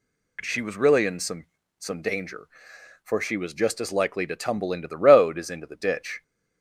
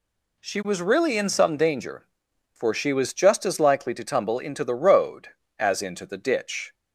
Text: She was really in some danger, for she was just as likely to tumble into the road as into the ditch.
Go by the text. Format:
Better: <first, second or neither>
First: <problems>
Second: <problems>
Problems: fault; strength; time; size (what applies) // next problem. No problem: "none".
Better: second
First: says "some" twice; at 1.7 s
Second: none